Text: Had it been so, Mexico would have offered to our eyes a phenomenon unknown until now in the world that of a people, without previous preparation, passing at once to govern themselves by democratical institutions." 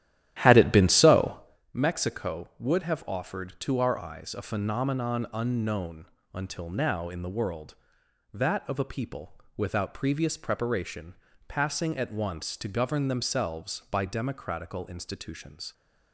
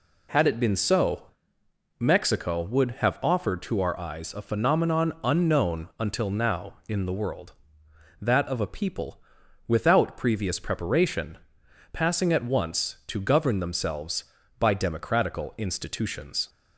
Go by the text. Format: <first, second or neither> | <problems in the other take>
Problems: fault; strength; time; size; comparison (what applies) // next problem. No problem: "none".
second | starts louder than the rest; strong; until 1.7 s; 12.5 dB // pauses between "unknown" and "until"; slight; at 6.0 s; 0.26 s long